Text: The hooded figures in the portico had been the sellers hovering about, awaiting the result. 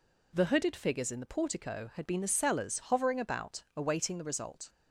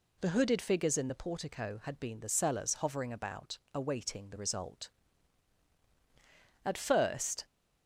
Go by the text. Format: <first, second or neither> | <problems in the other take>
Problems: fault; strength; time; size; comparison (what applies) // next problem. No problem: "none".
first | goes on to say "At first"; noticeable; from 6.6 s on; 0.80 s long